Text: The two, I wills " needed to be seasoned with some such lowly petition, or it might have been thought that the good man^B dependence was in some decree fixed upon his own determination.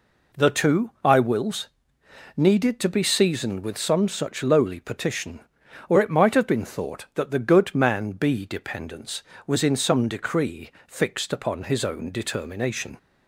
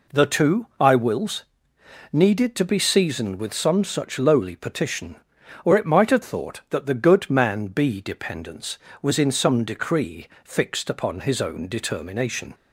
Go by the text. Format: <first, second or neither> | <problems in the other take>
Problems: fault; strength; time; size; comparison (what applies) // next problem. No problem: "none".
first | skips "been"; at 6.2 s // pauses between "decree" and "fixed"; slight; at 10.2 s; 0.16 s long; slight in the first